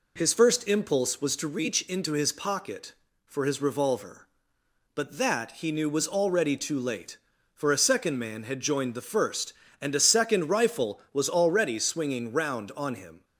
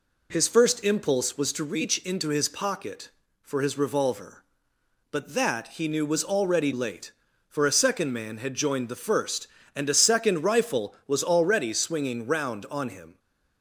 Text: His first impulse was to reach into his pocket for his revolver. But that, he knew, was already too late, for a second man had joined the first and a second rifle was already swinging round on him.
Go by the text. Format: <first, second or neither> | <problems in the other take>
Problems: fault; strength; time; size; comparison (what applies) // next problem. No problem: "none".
first | skips "too"; at 6.7 s